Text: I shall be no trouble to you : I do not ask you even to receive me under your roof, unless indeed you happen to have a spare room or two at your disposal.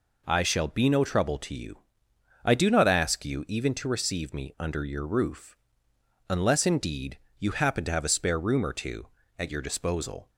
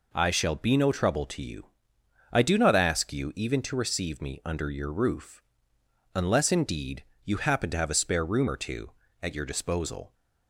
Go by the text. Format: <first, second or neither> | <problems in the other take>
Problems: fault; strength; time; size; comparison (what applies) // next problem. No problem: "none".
neither | pauses between "indeed" and "you"; slight; the same in both